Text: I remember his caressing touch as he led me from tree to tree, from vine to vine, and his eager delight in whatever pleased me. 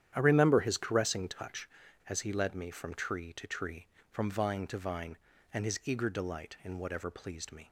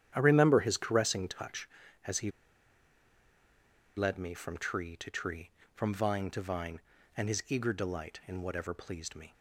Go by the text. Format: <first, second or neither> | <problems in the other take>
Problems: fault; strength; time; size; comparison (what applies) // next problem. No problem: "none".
first | starts louder than the rest; strong; until 1.1 s; 10 dB; strong in the first // pauses between "he" and "led"; strong; at 2.2 s; 1.6 s long